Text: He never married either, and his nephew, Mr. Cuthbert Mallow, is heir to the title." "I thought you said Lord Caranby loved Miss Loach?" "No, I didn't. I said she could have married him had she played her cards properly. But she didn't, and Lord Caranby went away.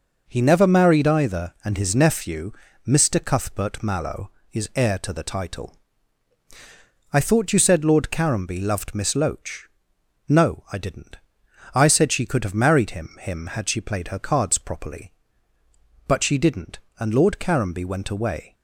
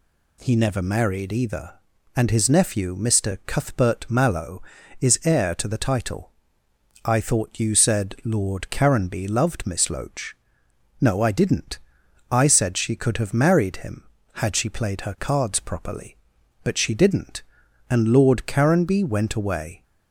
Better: second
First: says "him" twice; at 13.2 s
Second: none

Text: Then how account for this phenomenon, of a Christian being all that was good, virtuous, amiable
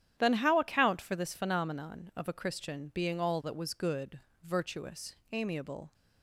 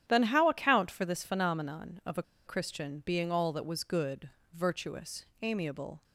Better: first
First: starts louder than the rest; strong; until 1.1 s; 10 dB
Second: starts louder than the rest; strong; until 1.0 s; 10.5 dB // pauses between "a" and "Christian"; slight; at 2.2 s; 0.24 s long

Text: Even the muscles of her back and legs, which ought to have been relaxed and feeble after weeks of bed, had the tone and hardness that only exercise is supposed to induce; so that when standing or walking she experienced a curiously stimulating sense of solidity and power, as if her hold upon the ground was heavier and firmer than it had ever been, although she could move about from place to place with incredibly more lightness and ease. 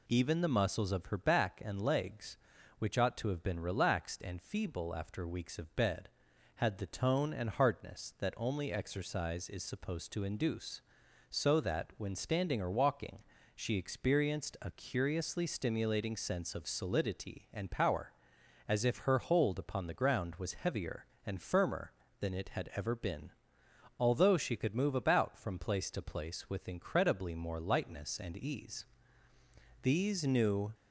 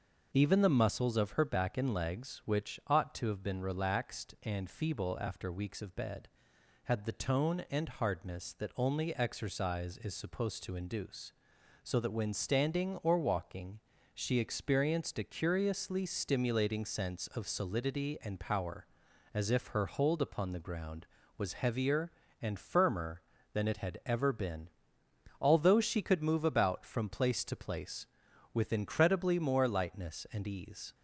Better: second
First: pauses between "walking" and "she"; slight; at 13.2 s; 0.32 s long // goes on to say "These new"; noticeable; from 29.8 s on; 0.92 s long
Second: pauses between "walking" and "she"; slight; at 13.7 s; 0.34 s long

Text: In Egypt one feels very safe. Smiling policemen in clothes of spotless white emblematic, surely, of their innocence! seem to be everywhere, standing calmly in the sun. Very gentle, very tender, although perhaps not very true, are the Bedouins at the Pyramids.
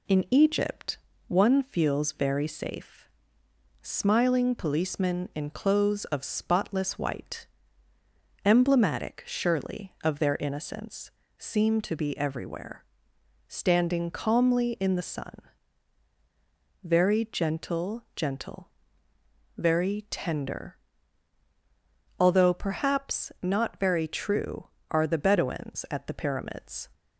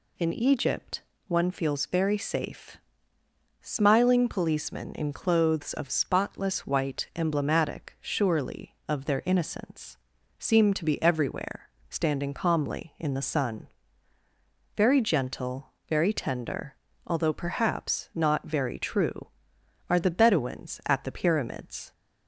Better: second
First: pauses between "Egypt" and "one"; slight; at 0.9 s; 0.30 s long // pauses between "white" and "emblematic"; at 7.4 s; 1.0 s long // says "gentle" twice; at 18.1 s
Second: pauses between "Egypt" and "one"; slight; at 1.0 s; 0.26 s long

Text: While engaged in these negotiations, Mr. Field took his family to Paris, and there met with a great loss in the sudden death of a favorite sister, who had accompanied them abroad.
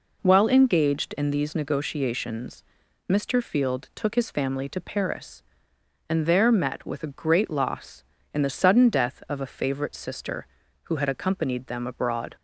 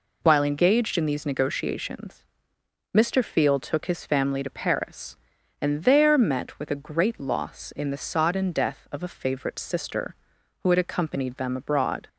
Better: first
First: none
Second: says "sodden" for "sudden"; at 7.9 s

